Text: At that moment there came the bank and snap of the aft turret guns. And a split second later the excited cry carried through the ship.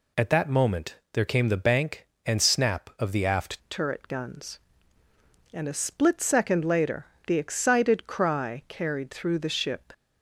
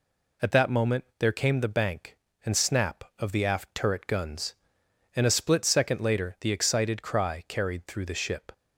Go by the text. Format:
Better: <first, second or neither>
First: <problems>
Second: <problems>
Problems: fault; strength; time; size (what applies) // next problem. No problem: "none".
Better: second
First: pauses between "moment" and "there"; slight; at 0.9 s; 0.18 s long // changes voice at "turret"; from 3.6 s on; 6.3 s long // pauses between "later" and "the"; slight; at 7.0 s; 0.20 s long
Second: none